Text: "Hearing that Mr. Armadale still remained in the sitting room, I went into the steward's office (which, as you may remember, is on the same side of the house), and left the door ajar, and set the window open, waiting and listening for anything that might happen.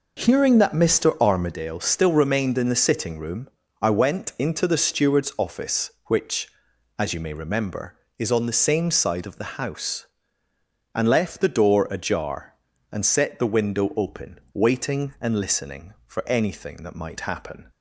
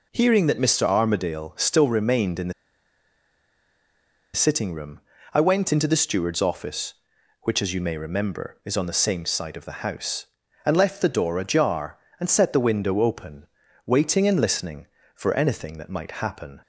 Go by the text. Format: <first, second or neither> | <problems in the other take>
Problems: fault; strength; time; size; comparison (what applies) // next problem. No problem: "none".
first | pauses between "the" and "sitting"; strong; at 2.5 s; 1.8 s long